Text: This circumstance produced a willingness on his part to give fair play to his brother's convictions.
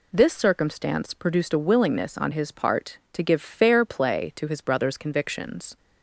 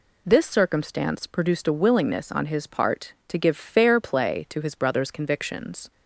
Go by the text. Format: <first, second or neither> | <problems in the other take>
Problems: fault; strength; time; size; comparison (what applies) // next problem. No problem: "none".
neither | none